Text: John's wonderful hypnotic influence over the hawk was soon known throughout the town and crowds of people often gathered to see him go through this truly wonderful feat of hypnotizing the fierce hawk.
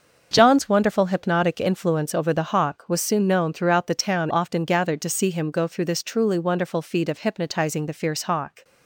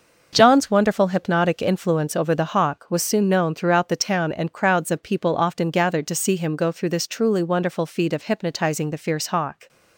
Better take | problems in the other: second | starts louder than the rest; until 1.3 s; 6.5 dB // skips "and crowds of people"; at 4.3 s

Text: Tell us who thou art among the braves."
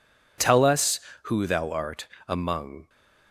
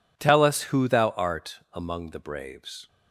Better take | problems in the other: second | pauses between "art" and "among"; slight; at 2.0 s; 0.20 s long // stops before "the braves"; at 2.8 s

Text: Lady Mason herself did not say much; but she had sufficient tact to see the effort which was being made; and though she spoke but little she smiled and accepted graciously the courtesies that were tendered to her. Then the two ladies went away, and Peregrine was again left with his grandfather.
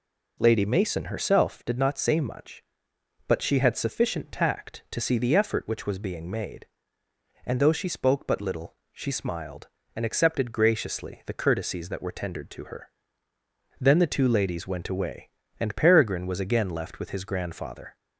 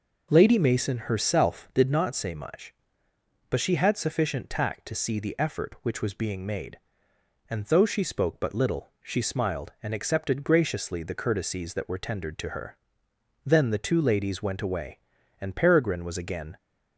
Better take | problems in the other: first | pauses between "little" and "she"; slight; at 8.8 s; 0.16 s long; slight in the first // stops before "left with his grandfather"; at 16.5 s

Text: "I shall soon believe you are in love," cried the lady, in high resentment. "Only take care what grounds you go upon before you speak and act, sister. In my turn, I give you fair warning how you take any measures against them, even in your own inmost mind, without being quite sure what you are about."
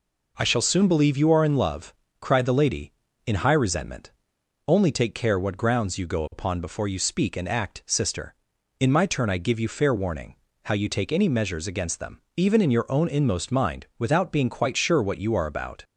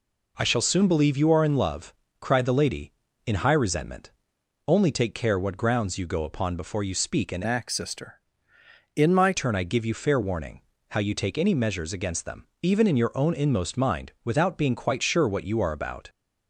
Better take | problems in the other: first | changes voice from "act" to "my"; from 7.4 to 9.3 s; 1.9 s long // pauses between "warning" and "how"; slight; at 10.6 s; 0.28 s long; slight in the first

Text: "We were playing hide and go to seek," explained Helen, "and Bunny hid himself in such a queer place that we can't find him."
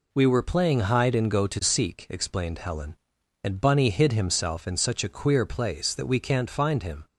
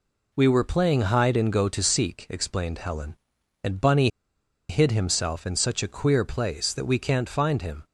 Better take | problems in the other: first | pauses between "Bunny" and "hid"; noticeable; at 4.0 s; 0.61 s long

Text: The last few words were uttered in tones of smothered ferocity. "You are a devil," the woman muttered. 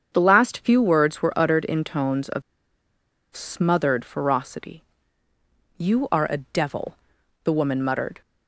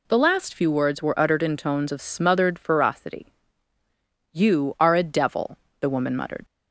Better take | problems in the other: second | starts louder than the rest; strong; until 1.1 s; 7.5 dB // pauses between "of" and "smothered"; noticeable; at 2.4 s; 0.92 s long

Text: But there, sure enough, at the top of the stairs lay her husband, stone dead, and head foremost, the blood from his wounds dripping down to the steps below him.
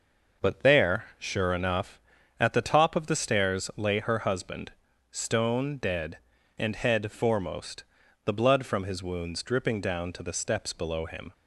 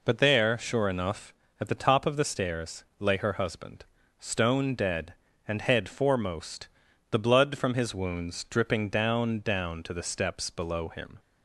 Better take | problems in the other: first | says "down" twice; at 9.3 s

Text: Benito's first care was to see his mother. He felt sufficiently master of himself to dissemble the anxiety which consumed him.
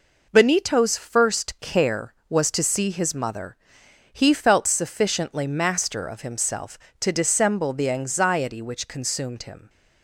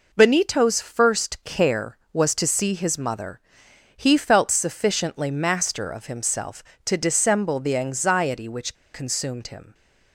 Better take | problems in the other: first | pauses between "which" and "consumed"; slight; at 8.7 s; 0.20 s long

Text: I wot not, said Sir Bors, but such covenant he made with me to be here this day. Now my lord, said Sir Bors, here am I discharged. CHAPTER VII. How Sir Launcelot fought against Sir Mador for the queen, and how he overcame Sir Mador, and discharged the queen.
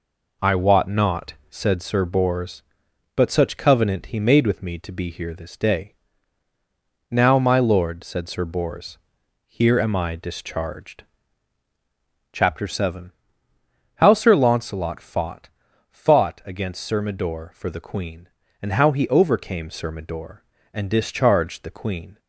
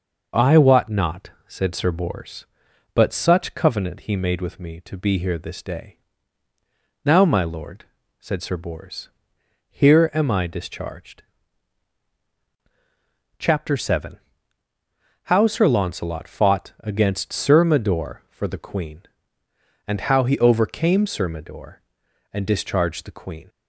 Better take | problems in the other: second | says "fought" twice; at 15.9 s

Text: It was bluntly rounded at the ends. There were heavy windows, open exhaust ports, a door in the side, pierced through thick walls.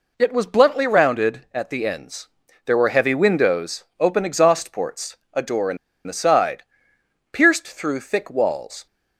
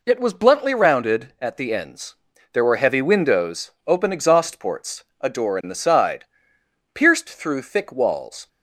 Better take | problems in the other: second | pauses between "in" and "the"; slight; at 5.7 s; 0.30 s long

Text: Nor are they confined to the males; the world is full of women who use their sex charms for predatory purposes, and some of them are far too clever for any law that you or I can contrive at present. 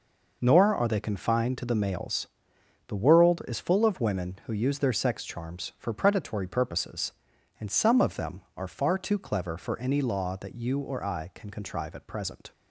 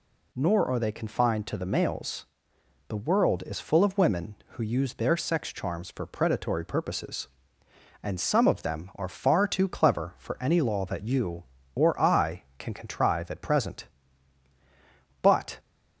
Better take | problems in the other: first | goes on to say "But"; slight; from 15.2 s on; 0.36 s long

